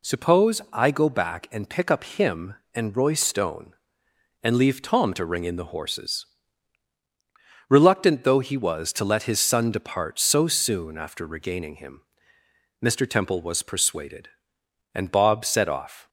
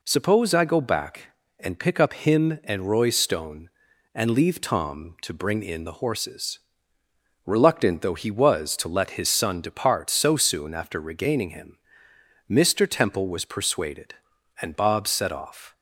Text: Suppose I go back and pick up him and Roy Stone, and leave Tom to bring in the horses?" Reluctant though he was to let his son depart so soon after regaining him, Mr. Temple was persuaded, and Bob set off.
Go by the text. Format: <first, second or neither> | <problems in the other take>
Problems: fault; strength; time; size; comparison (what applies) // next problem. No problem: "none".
second | says "ring" for "bring"; at 5.2 s